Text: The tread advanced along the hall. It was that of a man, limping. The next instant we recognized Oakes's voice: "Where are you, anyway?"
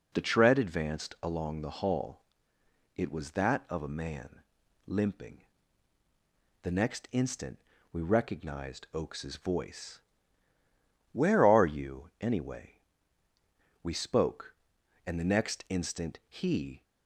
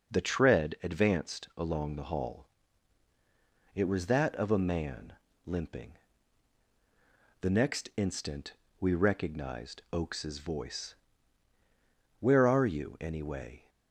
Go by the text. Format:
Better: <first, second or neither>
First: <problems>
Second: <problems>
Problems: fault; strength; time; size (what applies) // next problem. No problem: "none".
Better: second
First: pauses between "instant" and "we"; slight; at 7.5 s; 0.32 s long // goes on to say "We spoke and the next instant he"; strong; from 13.8 s on; 3.0 s long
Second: pauses between "instant" and "we"; slight; at 8.5 s; 0.26 s long